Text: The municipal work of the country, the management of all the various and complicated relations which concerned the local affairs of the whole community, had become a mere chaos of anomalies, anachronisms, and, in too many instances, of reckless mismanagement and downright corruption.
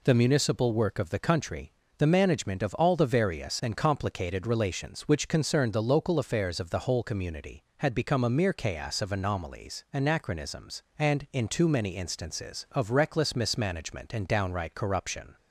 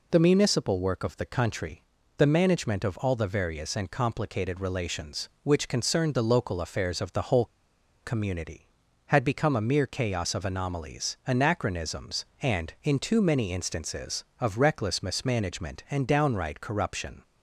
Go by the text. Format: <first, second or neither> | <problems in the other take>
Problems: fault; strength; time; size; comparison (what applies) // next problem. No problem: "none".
first | pauses between "whole" and "community"; noticeable; at 7.4 s; 0.58 s long